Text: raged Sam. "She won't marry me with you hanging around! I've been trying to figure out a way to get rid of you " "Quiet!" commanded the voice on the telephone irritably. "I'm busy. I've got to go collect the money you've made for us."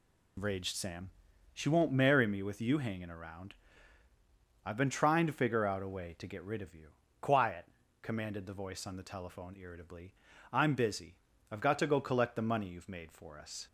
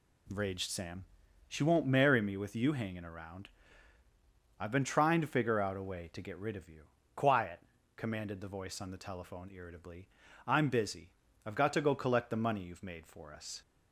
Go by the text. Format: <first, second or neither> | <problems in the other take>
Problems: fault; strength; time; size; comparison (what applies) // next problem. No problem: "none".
second | loses the start of "raged"; at 0.3 s; 55 ms